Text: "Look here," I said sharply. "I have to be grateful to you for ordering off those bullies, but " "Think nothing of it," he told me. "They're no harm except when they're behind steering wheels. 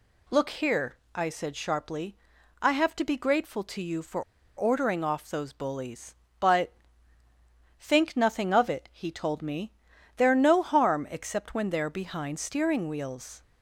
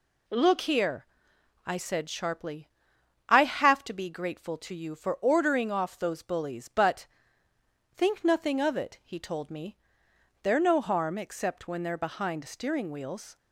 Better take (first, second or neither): second